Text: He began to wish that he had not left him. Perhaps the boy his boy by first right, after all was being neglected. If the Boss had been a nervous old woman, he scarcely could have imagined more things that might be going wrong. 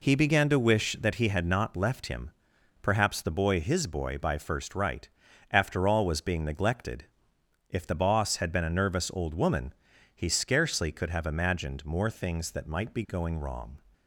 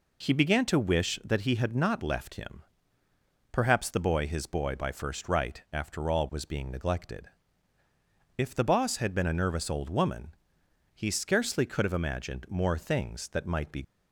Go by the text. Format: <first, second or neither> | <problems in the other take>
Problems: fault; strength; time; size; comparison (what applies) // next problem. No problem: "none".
first | stops before "going wrong"; at 13.8 s